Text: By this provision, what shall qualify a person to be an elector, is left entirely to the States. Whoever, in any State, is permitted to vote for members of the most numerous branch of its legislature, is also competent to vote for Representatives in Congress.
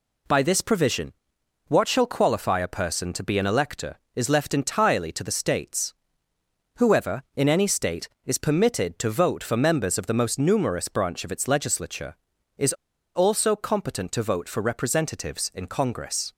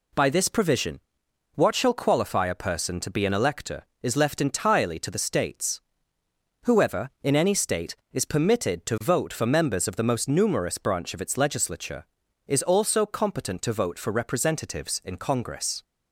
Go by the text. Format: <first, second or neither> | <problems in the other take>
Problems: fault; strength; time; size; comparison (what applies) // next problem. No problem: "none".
second | pauses between "is" and "also"; at 12.7 s; 0.42 s long